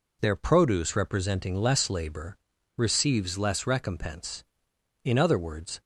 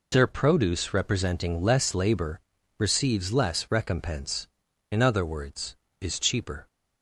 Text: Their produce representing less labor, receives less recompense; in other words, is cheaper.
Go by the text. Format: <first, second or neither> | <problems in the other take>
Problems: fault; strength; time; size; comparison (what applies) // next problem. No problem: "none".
second | stops before "is cheaper"; at 5.8 s